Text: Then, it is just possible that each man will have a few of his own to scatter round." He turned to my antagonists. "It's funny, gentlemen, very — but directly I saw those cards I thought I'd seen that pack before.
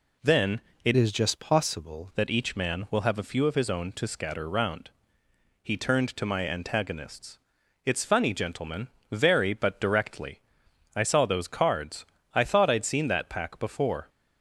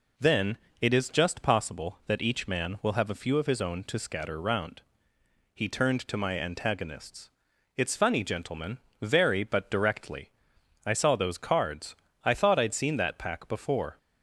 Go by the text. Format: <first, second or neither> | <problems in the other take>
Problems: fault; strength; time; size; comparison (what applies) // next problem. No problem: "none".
second | changes voice from "is" to "possible"; from 0.9 to 2.1 s; 1.2 s long // pauses between "directly" and "I"; noticeable; at 10.4 s; 0.56 s long; noticeable in the second // pauses between "cards" and "I"; slight; at 12.0 s; 0.26 s long; slight in the second